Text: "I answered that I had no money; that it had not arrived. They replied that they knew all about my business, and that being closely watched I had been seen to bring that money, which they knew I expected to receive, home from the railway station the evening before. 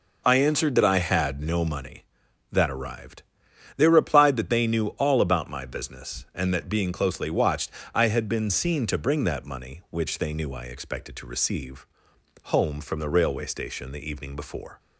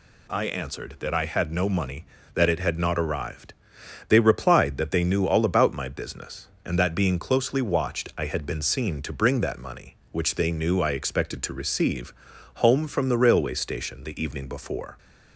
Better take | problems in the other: second | skips "it had not"; at 2.7 s // pauses between "watched" and "I"; slight; at 7.7 s; 0.22 s long

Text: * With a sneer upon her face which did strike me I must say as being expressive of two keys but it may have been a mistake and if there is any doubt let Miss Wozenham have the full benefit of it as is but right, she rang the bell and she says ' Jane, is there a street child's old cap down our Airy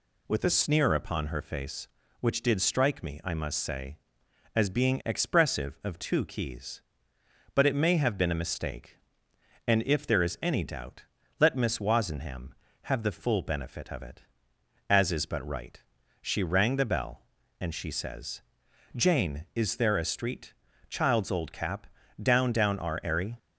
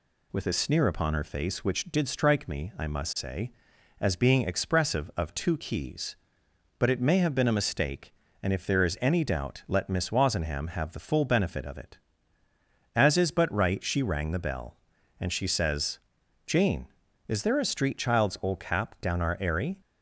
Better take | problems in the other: second | pauses between "doubt" and "let"; slight; at 11.0 s; 0.36 s long // pauses between "street" and "child's"; at 20.5 s; 0.38 s long // pauses between "cap" and "down"; slight; at 21.8 s; 0.36 s long // says "down" twice; at 22.5 s

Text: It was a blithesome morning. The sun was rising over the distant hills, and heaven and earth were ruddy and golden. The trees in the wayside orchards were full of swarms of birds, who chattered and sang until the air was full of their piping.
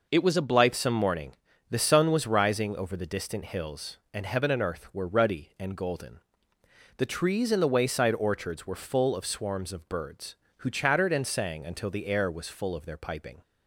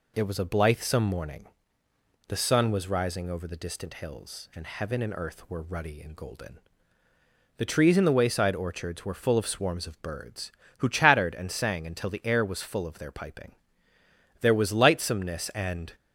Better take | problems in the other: first | goes on to say "There was lightsomeness and"; from 14.3 s on; 1.5 s long

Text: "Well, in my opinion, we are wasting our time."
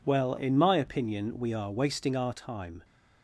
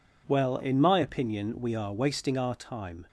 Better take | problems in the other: neither | none

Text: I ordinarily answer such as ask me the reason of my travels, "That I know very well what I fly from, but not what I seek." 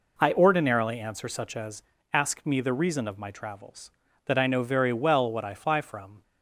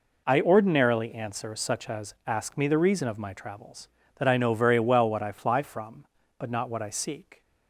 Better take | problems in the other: second | pauses between "as" and "ask"; slight; at 1.8 s; 0.30 s long // stops before "but not what I seek"; at 6.2 s

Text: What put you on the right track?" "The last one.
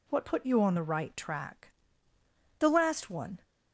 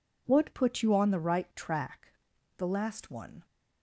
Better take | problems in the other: neither | none

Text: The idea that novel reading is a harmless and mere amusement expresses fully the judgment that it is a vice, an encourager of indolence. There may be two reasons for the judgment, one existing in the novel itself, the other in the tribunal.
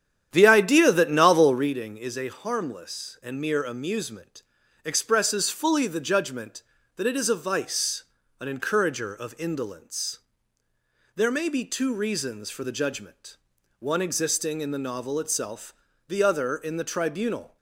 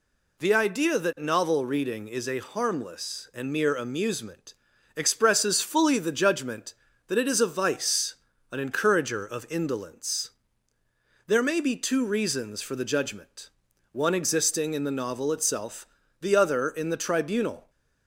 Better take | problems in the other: second | starts louder than the rest; strong; until 1.7 s; 9.5 dB // pauses between "amusement" and "expresses"; at 4.4 s; 0.42 s long; also in the second

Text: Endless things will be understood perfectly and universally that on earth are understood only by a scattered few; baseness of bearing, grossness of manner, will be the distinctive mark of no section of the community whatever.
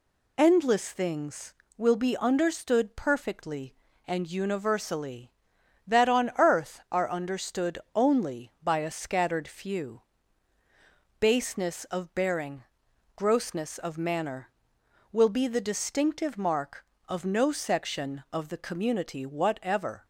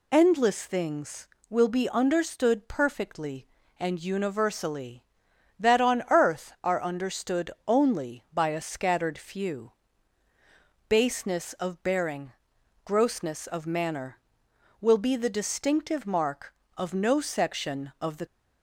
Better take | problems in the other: first | pauses between "understood" and "only"; slight; at 7.4 s; 0.16 s long; slight in the first // stops before "community whatever"; at 18.2 s

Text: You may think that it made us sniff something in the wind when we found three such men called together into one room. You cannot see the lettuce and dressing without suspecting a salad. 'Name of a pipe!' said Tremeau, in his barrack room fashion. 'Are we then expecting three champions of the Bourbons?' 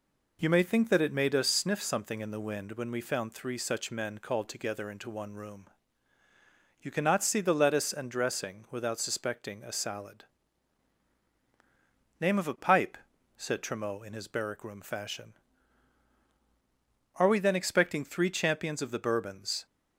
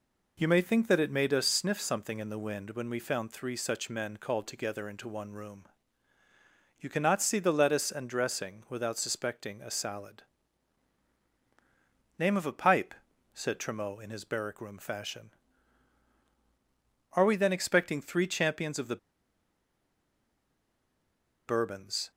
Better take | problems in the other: first | pauses between "the" and "Bourbons"; strong; at 18.9 s; 2.5 s long

